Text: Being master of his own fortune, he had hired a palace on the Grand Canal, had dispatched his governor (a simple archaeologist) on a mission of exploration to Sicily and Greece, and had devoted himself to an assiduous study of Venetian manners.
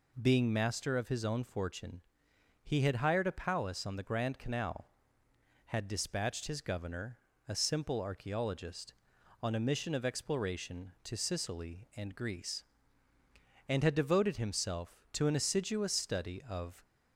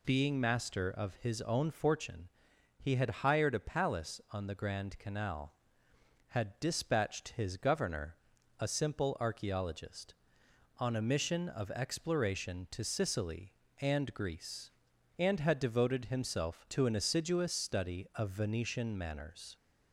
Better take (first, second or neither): second